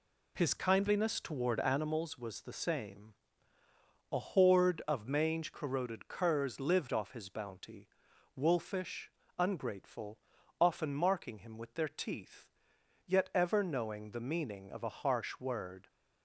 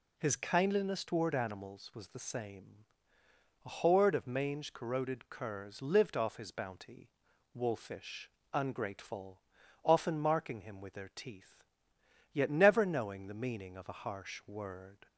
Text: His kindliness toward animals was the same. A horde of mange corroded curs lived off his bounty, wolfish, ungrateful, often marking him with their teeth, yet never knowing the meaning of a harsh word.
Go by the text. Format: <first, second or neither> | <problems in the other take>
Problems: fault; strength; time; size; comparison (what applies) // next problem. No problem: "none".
second | says "ever" for "never"; at 13.3 s